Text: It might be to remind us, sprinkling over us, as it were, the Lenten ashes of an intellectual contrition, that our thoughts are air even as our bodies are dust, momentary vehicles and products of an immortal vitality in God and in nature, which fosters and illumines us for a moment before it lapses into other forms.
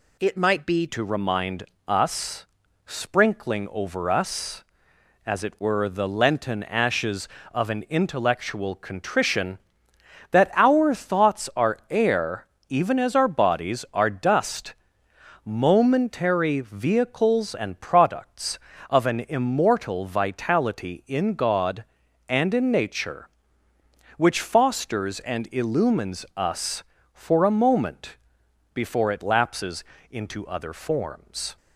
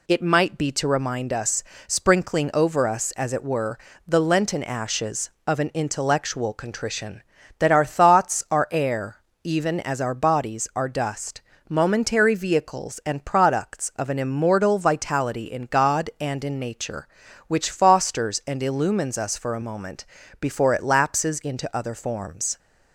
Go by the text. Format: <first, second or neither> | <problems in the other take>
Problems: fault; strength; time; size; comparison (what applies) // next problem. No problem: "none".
second | changes voice at "to"; from 0.8 s on; 30.7 s long // pauses between "remind" and "us"; slight; at 1.6 s; 0.24 s long // pauses between "air" and "even"; slight; at 12.4 s; 0.22 s long; slight in the second // pauses between "moment" and "before"; noticeable; at 28.1 s; 0.58 s long; also in the second // pauses between "lapses" and "into"; slight; at 29.8 s; 0.28 s long